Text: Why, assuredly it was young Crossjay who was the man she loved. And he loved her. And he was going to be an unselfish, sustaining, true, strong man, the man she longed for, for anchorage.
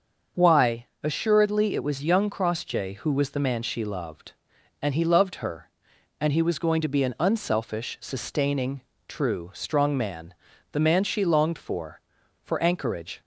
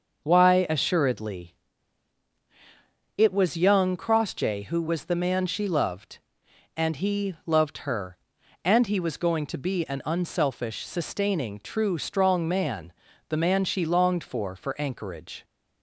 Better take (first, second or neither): first